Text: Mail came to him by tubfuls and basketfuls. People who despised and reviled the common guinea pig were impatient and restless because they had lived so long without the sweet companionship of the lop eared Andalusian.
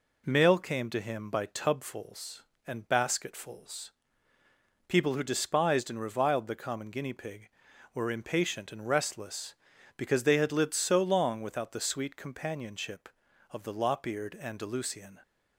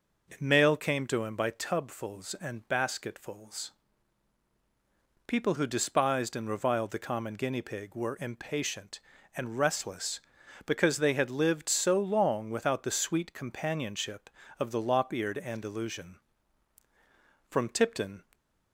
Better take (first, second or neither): first